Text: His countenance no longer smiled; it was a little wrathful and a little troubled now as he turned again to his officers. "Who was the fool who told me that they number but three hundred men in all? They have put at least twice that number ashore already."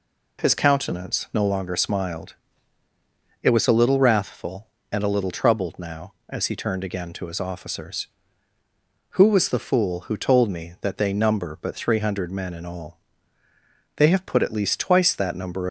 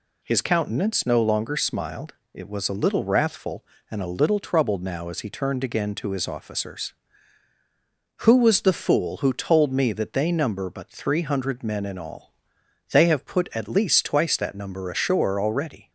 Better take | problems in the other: second | stops before "ashore already"; at 15.6 s

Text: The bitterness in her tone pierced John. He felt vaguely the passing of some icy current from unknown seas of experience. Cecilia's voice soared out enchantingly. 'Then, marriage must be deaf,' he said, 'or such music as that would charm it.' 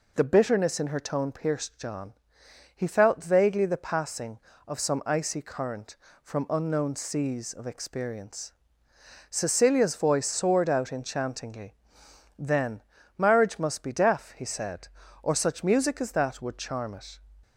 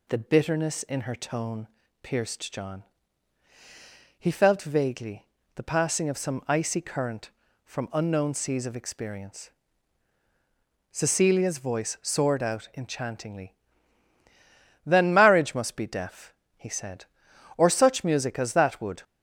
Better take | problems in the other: first | pauses between "tone" and "pierced"; slight; at 1.6 s; 0.34 s long // pauses between "vaguely" and "the"; slight; at 5.2 s; 0.28 s long // stops before "charm it"; at 19.0 s

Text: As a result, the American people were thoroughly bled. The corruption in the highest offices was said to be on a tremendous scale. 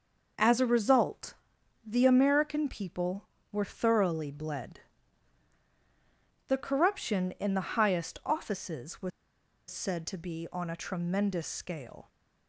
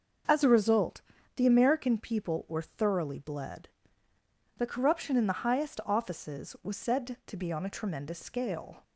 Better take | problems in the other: second | starts louder than the rest; noticeable; until 1.9 s; 6 dB; also in the second // pauses between "was" and "said"; noticeable; at 9.1 s; 0.60 s long

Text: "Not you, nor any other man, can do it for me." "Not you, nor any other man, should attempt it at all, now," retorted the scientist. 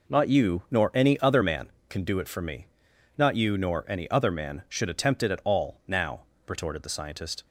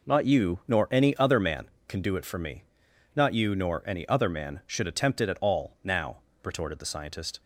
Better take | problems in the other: neither | none

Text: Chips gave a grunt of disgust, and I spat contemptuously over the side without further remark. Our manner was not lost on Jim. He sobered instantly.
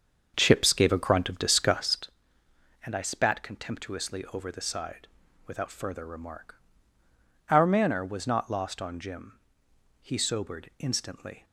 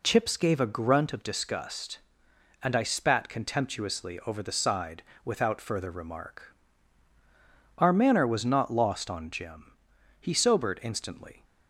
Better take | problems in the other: second | starts louder than the rest; until 2.1 s; 7 dB // pauses between "side" and "without"; at 5.0 s; 0.38 s long; slight in the second

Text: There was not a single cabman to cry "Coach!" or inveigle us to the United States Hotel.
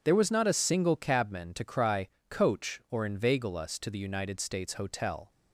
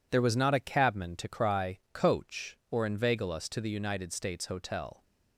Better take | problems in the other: first | skips "single"; at 0.5 s // pauses between "cry" and "Coach"; slight; at 1.7 s; 0.16 s long; slight in the first

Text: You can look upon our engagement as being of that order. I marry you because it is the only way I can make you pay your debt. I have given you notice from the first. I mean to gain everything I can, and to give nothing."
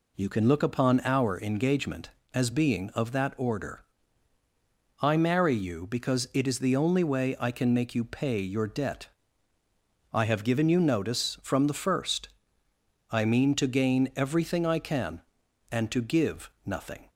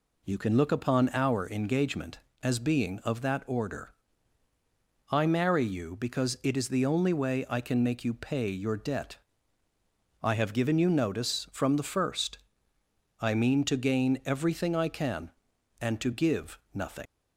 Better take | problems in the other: first | leaves "nothing" unfinished; at 17.0 s; 125 ms

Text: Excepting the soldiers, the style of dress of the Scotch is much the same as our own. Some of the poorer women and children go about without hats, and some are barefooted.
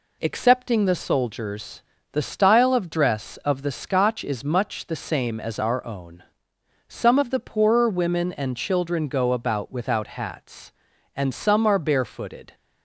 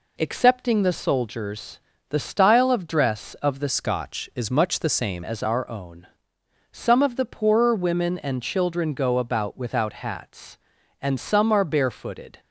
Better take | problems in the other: first | changes voice from "Scotch" to "same"; from 3.6 to 5.2 s; 1.6 s long

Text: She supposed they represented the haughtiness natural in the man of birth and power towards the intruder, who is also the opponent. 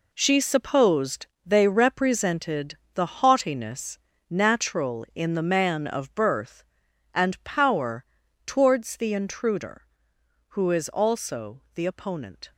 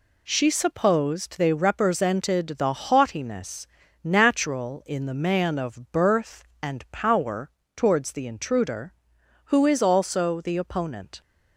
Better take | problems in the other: second | gets quieter; strong; throughout; 10 dB // pauses between "supposed" and "they"; slight; at 1.2 s; 0.18 s long // pauses between "represented" and "the"; slight; at 2.7 s; 0.18 s long // pauses between "haughtiness" and "natural"; slight; at 3.9 s; 0.30 s long; slight in the second // pauses between "power" and "towards"; at 8.0 s; 0.42 s long; slight in the second

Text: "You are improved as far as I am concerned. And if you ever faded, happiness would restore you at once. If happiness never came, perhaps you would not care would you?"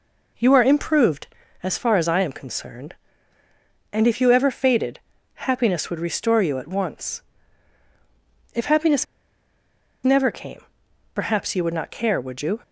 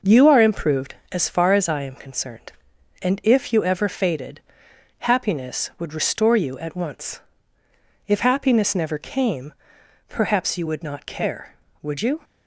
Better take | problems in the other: second | pauses between "happiness" and "never"; at 9.0 s; 0.98 s long

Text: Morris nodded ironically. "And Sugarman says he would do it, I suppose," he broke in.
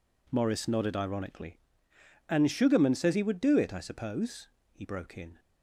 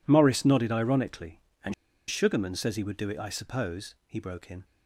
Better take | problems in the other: first | pauses between "And" and "Sugarman"; at 1.7 s; 0.36 s long

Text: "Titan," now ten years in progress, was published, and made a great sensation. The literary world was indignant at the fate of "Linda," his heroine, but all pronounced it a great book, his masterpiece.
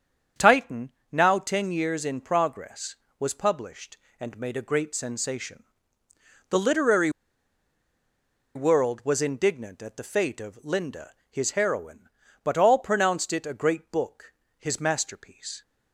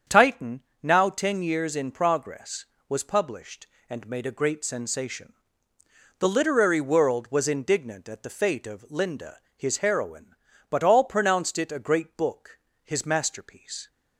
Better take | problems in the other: second | starts louder than the rest; strong; until 1.5 s; 8 dB; strong in the second // pauses between "literary" and "world"; strong; at 7.0 s; 1.4 s long

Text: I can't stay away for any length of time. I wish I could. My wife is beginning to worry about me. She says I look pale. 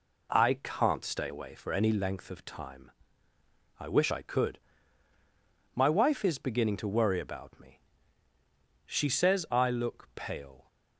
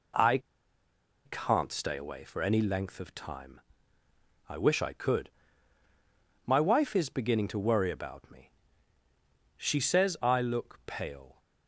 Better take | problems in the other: first | pauses between "I" and "can't"; noticeable; at 0.3 s; 0.86 s long

